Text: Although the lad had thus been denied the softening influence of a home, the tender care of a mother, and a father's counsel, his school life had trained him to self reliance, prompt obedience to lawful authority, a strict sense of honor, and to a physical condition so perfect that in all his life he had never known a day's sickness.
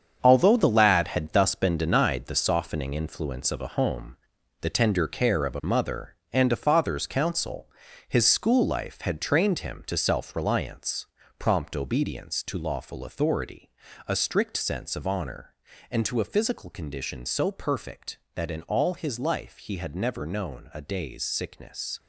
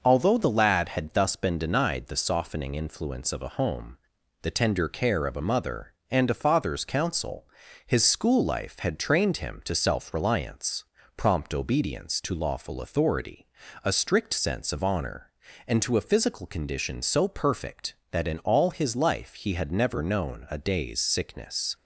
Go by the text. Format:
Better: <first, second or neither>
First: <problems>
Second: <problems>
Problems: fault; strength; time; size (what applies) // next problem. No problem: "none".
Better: second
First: gets quieter; strong; throughout; 9 dB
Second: none